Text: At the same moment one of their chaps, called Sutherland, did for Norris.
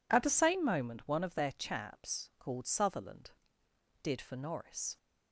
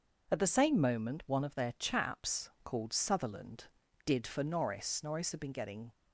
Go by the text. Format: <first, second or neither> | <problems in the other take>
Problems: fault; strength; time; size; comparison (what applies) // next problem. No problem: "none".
first | goes on to say "Norris had been getting"; noticeable; from 5.0 s on; 0.92 s long